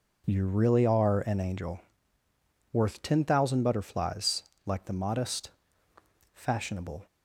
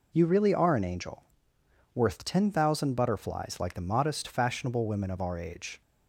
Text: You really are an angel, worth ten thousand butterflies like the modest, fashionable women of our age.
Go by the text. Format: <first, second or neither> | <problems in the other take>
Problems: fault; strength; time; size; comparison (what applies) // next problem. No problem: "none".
second | pauses between "butterflies" and "like"; slight; at 4.4 s; 0.16 s long // stops before "women of our age"; at 7.0 s